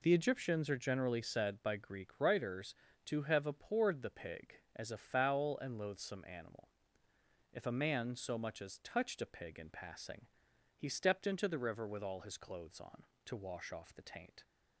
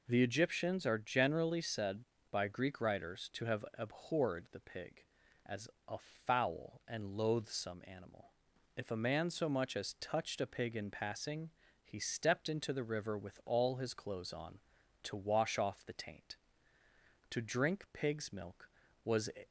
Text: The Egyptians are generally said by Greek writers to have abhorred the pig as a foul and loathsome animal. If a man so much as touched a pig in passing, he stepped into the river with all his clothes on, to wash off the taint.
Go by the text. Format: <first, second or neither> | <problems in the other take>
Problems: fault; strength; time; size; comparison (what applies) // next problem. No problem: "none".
first | pauses between "as" and "a"; slight; at 5.6 s; 0.20 s long // pauses between "a" and "foul"; slight; at 5.9 s; 0.30 s long // goes on to say "To drink pig's milk was"; strong; from 17.2 s on; 2.0 s long